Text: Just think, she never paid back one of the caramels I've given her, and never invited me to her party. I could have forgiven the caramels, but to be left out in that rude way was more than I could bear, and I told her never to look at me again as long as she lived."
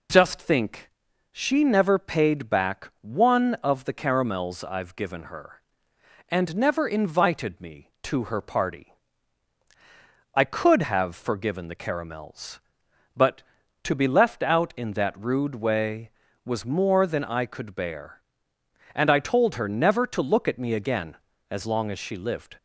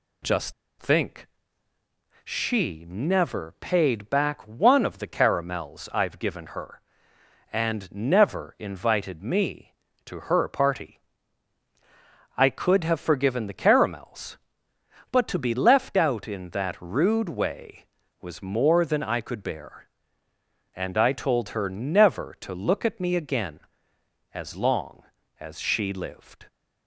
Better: first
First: none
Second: pauses between "Just" and "think"; slight; at 0.5 s; 0.28 s long

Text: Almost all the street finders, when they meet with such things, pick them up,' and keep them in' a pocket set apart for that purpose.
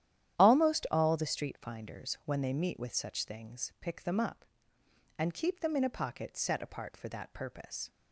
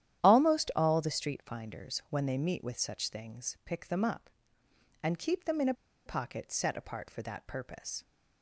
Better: first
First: starts louder than the rest; strong; until 1.4 s; 11 dB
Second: starts louder than the rest; strong; until 1.2 s; 11 dB // pauses between "a" and "pocket"; slight; at 5.7 s; 0.32 s long

